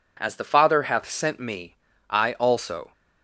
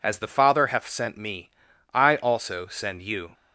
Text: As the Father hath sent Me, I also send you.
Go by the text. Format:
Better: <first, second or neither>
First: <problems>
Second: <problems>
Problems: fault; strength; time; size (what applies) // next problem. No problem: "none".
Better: second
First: stops before "send you"; at 2.9 s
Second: none